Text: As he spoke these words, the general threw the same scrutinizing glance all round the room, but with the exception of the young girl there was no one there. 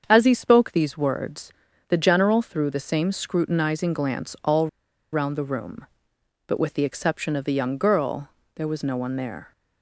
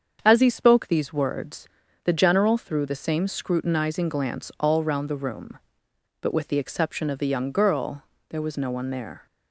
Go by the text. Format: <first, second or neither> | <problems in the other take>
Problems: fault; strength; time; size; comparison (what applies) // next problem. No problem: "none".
second | starts louder than the rest; strong; until 1.0 s; 7.5 dB; strong in the second // pauses between "all" and "round"; at 4.6 s; 0.44 s long // pauses between "girl" and "there"; slight; at 8.2 s; 0.26 s long; slight in the second